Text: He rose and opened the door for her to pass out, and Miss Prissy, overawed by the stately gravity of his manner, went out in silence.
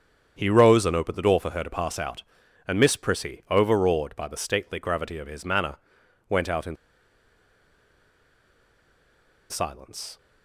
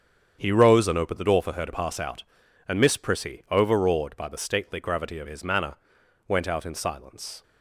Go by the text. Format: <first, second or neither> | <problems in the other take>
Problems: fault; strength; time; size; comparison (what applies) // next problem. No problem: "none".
second | starts louder than the rest; strong; until 1.3 s; 8 dB; strong in the second // pauses between "in" and "silence"; strong; at 6.7 s; 2.7 s long